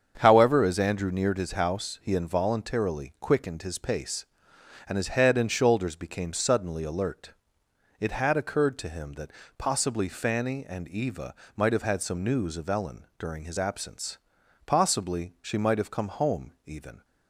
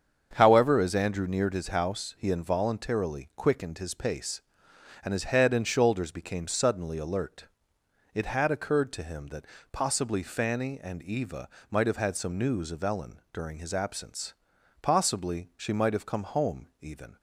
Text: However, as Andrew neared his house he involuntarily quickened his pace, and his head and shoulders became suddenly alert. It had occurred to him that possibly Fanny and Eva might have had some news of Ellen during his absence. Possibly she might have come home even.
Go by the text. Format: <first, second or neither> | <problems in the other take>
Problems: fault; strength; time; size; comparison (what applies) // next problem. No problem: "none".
neither | starts louder than the rest; strong; the same in both // pauses between "that" and "possibly"; slight; the same in both // pauses between "Eva" and "might"; slight; the same in both